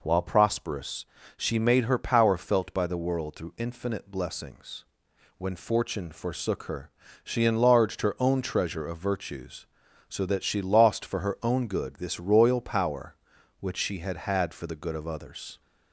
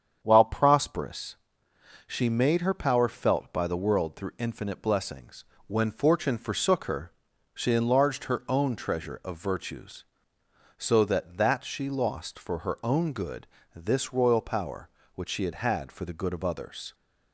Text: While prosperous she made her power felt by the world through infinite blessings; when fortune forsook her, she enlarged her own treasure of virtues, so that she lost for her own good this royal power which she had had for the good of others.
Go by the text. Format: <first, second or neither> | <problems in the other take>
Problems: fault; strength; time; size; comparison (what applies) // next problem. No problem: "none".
first | starts louder than the rest; strong; until 1.2 s; 8 dB // pauses between "prosperous" and "she"; noticeable; at 1.3 s; 0.70 s long; slight in the first // says "that" twice; at 11.3 s // pauses between "good" and "this"; slight; at 13.4 s; 0.26 s long